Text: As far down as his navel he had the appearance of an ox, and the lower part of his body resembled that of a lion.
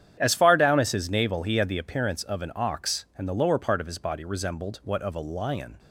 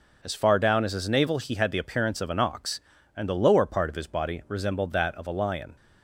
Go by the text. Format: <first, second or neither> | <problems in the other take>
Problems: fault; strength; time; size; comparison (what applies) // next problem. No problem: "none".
second | starts louder than the rest; strong; until 1.2 s; 9.5 dB // says "what" for "that"; at 4.8 s